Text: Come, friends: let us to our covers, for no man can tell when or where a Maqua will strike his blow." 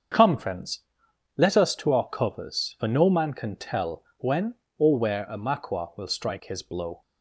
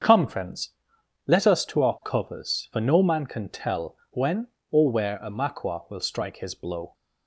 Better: neither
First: starts louder than the rest; until 1.7 s; 7 dB // pauses between "tell" and "when"; slight; at 4.0 s; 0.16 s long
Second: starts louder than the rest; strong; until 1.6 s; 7 dB // pauses between "tell" and "when"; slight; at 3.9 s; 0.16 s long

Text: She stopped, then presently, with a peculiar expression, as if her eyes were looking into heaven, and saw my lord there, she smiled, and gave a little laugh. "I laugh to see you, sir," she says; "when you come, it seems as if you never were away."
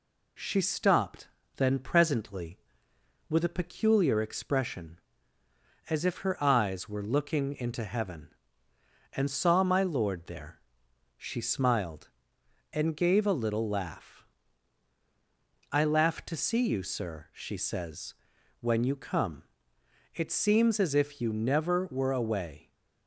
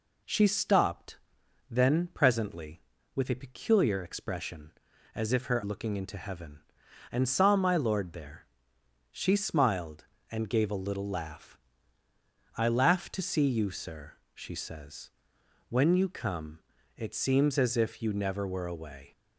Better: first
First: none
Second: skips "eyes were"; at 5.6 s

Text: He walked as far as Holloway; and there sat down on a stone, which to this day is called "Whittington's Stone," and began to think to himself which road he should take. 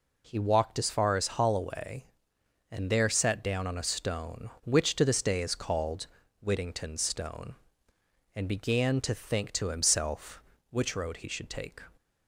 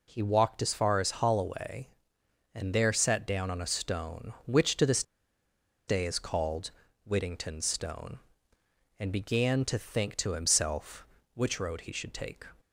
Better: first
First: pauses between "called" and "Whittington's"; slight; at 6.0 s; 0.36 s long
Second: pauses between "this" and "day"; noticeable; at 5.0 s; 0.84 s long // pauses between "called" and "Whittington's"; slight; at 6.6 s; 0.36 s long

